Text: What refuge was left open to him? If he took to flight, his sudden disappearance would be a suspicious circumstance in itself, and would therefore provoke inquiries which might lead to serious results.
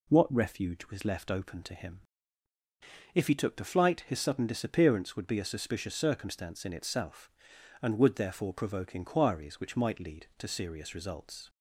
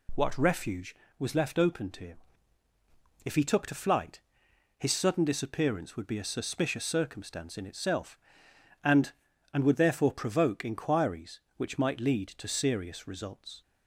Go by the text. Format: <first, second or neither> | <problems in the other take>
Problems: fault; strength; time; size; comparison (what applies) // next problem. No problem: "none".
first | says "and" twice; at 9.5 s